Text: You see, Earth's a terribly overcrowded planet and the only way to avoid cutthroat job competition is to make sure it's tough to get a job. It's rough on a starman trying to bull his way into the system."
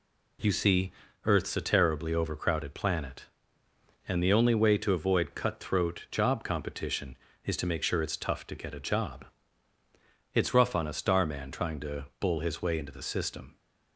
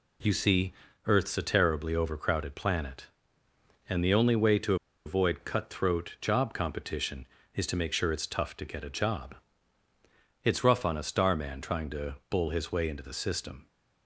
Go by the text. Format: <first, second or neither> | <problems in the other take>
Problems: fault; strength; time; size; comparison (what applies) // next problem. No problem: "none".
first | pauses between "to" and "avoid"; slight; at 4.7 s; 0.30 s long